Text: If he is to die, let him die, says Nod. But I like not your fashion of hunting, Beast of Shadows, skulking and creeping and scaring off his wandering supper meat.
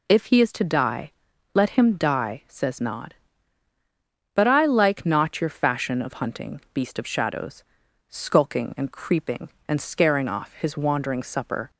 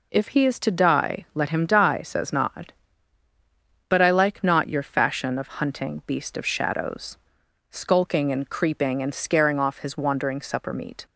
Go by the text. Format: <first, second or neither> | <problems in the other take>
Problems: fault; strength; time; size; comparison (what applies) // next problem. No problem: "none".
second | stops before "meat"; at 11.6 s